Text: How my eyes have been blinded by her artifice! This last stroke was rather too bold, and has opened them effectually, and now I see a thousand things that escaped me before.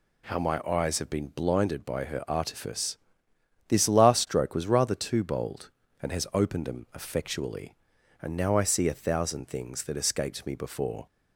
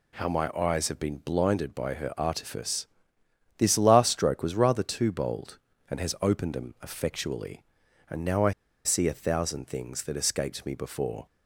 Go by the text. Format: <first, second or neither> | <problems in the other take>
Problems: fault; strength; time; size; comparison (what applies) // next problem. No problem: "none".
first | pauses between "I" and "see"; slight; at 8.5 s; 0.33 s long